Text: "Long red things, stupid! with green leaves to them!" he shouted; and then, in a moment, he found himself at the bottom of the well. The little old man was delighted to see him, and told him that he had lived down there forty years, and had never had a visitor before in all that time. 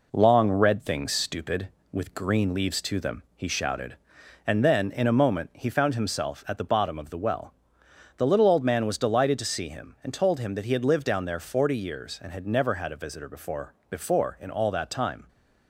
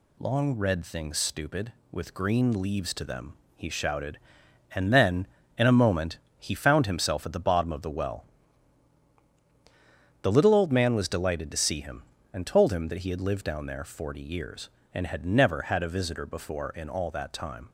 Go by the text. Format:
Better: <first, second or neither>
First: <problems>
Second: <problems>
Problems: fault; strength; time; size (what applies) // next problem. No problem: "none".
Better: second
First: says "before" twice; at 13.8 s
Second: none